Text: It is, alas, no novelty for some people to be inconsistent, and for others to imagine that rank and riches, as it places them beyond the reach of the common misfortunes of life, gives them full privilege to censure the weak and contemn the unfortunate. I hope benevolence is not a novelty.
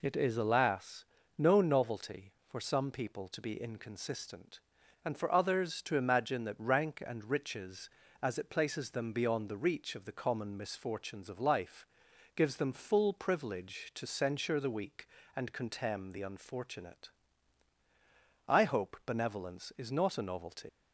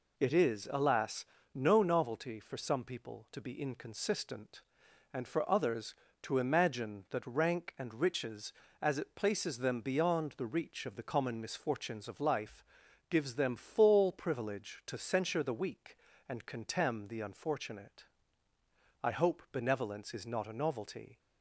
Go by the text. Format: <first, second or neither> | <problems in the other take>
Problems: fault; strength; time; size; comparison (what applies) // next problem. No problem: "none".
second | leaves "novelty" unfinished; at 20.6 s; 110 ms